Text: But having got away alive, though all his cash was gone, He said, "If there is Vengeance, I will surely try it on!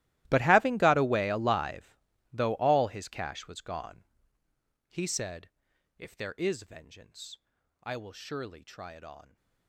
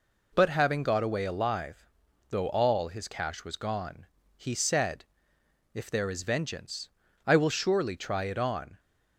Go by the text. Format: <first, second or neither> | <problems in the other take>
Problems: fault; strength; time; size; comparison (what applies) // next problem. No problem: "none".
second | gets quieter; strong; throughout; 20.5 dB